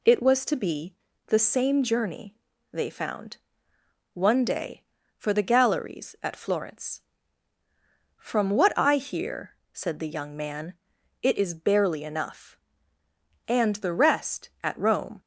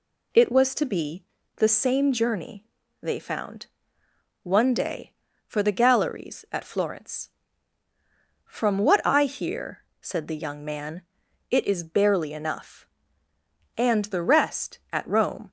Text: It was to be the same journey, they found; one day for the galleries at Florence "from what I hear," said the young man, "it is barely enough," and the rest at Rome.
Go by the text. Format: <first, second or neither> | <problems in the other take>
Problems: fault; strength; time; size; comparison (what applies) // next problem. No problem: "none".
neither | pauses between "be" and "the"; slight; the same in both